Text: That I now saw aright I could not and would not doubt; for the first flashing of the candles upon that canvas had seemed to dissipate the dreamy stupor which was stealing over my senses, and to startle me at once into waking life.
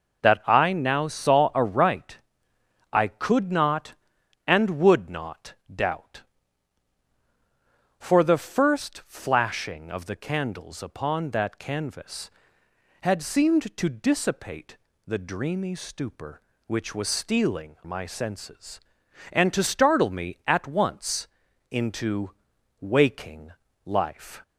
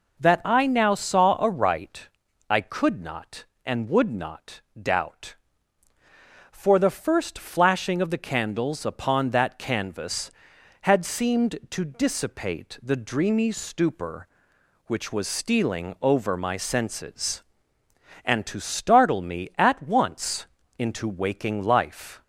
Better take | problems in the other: second | pauses between "aright" and "I"; noticeable; at 2.1 s; 0.74 s long; also in the second // pauses between "not" and "doubt"; slight; at 5.5 s; 0.18 s long; slight in the second // pauses between "dissipate" and "the"; slight; at 14.7 s; 0.30 s long // skips "over"; at 17.8 s // pauses between "once" and "into"; at 21.2 s; 0.44 s long; slight in the second // pauses between "into" and "waking"; noticeable; at 22.3 s; 0.50 s long // pauses between "waking" and "life"; slight; at 23.5 s; 0.32 s long

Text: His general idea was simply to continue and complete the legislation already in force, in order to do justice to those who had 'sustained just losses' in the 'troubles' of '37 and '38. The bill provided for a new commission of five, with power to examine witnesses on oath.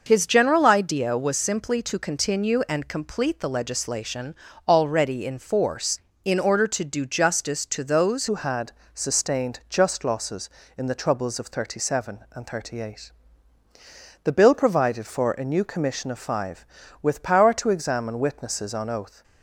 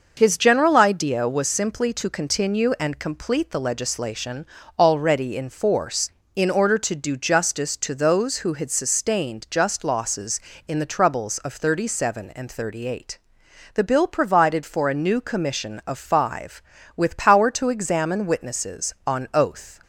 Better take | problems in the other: second | pauses between "legislation" and "already"; slight; at 4.3 s; 0.30 s long; slight in the second // changes voice at "who"; from 8.2 s on; 11.0 s long // pauses between "had" and "sustained"; slight; at 8.7 s; 0.20 s long

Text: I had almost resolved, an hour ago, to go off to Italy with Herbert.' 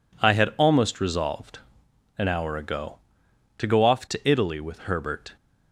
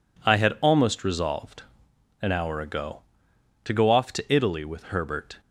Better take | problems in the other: neither | none

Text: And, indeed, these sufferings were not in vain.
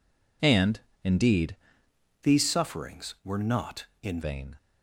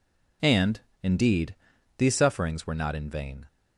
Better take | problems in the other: second | changes voice from "these" to "in"; from 2.2 to 4.1 s; 1.9 s long

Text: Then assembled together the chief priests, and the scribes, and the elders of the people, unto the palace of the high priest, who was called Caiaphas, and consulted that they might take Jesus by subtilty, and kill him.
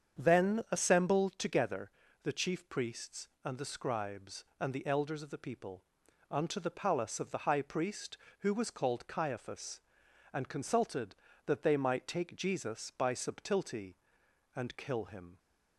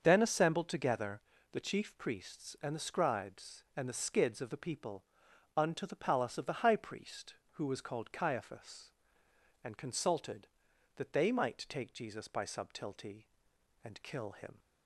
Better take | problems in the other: first | starts louder than the rest; until 1.0 s; 7 dB; strong in the first // pauses between "together" and "the"; slight; at 1.2 s; 0.30 s long; slight in the first // says "skids" for "elders"; at 3.9 s

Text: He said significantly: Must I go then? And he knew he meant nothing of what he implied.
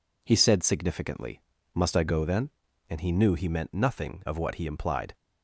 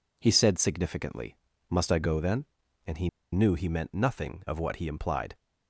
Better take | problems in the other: first | pauses between "he" and "knew"; slight; at 3.0 s; 0.25 s long

